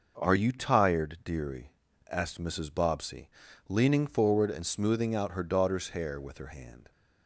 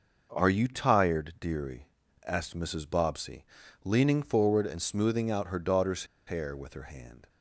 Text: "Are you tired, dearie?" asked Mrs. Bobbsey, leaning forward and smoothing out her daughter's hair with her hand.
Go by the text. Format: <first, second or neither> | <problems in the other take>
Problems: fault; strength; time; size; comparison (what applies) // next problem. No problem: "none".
first | pauses between "daughter's" and "hair"; slight; at 6.0 s; 0.22 s long